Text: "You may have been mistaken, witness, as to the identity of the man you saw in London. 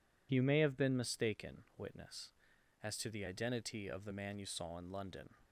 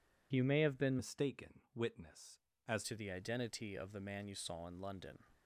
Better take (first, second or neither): first